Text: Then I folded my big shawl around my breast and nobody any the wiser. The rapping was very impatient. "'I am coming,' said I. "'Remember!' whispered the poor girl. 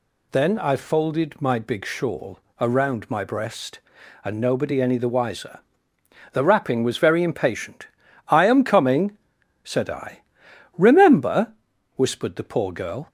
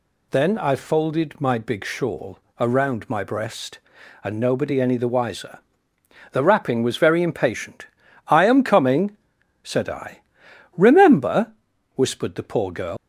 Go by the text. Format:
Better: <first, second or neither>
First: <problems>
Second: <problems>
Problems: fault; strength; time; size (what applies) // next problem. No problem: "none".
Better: first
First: pauses between "shawl" and "around"; slight; at 2.3 s; 0.22 s long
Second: pauses between "shawl" and "around"; slight; at 2.3 s; 0.22 s long // leaves "girl" unfinished; at 12.9 s; 115 ms